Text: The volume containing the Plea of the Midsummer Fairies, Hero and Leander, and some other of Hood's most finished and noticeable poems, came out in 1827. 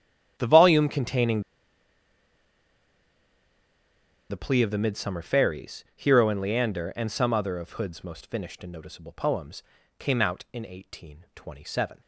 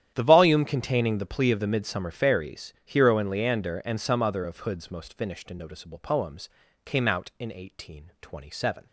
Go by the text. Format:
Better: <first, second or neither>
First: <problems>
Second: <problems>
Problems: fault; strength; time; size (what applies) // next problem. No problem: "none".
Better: second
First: starts louder than the rest; strong; until 1.3 s; 10.5 dB // pauses between "containing" and "the"; strong; at 1.4 s; 2.8 s long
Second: starts louder than the rest; strong; until 1.1 s; 10.5 dB